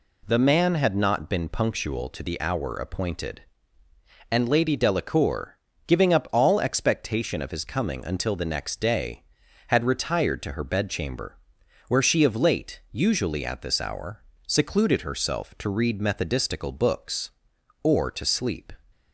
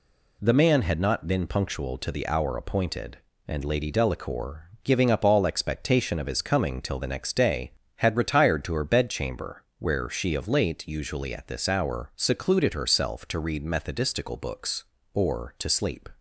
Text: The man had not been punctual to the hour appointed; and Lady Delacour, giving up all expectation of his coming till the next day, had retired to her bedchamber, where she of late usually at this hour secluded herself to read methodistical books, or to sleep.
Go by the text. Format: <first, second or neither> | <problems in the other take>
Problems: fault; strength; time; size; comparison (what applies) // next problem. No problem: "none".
second | says "until" for "till"; at 8.0 s // pauses between "hour" and "secluded"; slight; at 14.2 s; 0.24 s long